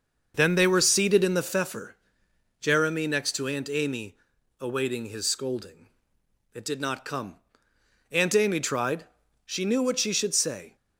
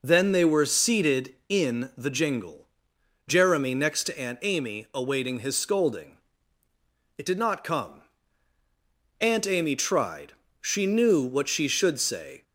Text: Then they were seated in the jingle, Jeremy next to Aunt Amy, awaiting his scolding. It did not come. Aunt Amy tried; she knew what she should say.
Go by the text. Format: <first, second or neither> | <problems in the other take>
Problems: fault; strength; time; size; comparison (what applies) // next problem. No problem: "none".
second | starts louder than the rest; until 1.3 s; 6 dB // says "pfeffer" for "jingle"; at 1.4 s